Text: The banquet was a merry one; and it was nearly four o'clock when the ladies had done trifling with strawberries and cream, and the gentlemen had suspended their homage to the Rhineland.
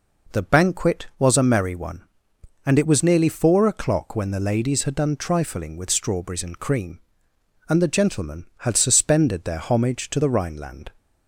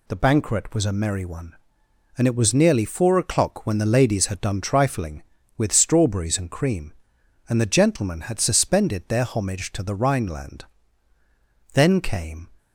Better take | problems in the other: first | goes on to say "Then came"; noticeable; from 11.7 s on; 0.74 s long

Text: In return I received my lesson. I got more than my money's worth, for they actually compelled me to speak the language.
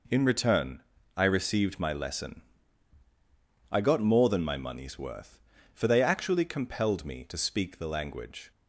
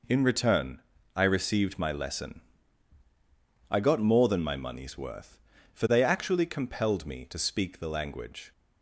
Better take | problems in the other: neither | pauses between "return" and "I"; slight; the same in both

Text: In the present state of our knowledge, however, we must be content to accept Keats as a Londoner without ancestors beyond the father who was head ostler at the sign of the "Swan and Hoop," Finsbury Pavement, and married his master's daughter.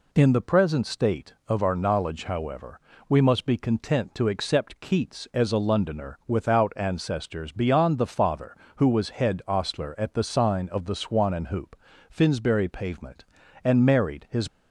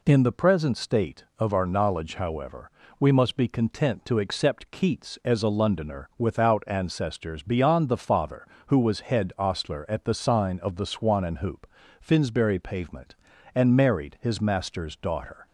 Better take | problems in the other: second | stops before "master's daughter"; at 14.4 s

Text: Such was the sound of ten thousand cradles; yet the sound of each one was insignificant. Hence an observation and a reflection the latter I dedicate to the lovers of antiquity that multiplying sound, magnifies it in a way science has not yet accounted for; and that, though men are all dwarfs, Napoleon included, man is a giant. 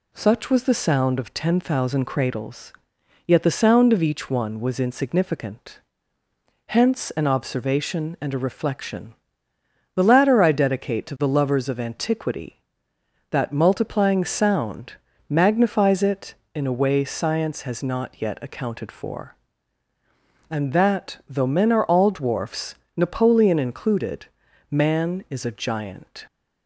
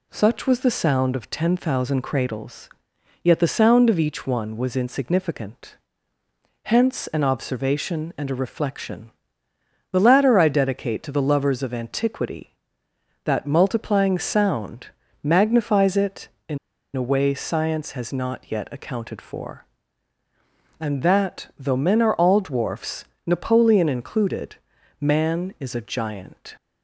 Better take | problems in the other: first | pauses between "reflection" and "the"; noticeable; at 9.1 s; 0.80 s long; noticeable in the first // pauses between "in" and "a"; at 16.5 s; 0.37 s long

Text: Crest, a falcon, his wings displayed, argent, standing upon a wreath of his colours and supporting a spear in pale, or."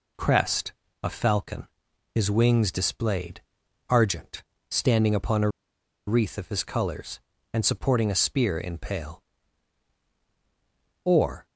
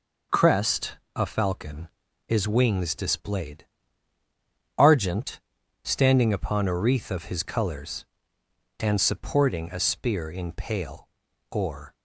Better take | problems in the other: second | pauses between "a" and "wreath"; noticeable; at 5.4 s; 0.58 s long

